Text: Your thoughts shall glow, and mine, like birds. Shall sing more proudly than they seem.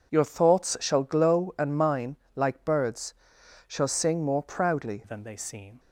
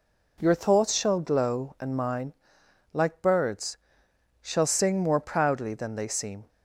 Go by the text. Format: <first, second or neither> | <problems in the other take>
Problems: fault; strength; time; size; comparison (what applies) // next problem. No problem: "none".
second | changes voice at "than"; from 5.0 s on; 0.7 s long